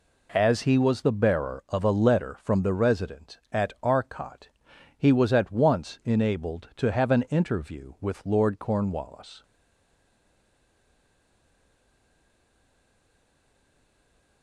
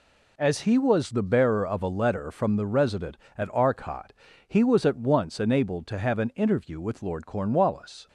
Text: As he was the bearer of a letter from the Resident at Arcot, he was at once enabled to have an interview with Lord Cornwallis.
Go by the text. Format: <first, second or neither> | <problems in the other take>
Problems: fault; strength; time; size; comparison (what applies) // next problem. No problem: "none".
second | stays silent after the last word; strong; from 9.4 s on; 5.0 s long